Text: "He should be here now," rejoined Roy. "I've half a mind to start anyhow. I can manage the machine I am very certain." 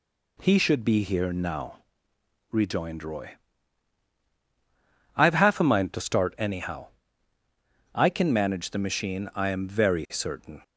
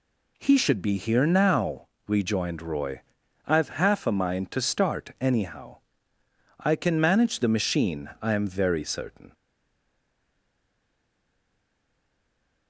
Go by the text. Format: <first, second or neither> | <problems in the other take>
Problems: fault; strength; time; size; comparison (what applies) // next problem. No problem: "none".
first | stays silent after the last word; strong; from 9.3 s on; 3.3 s long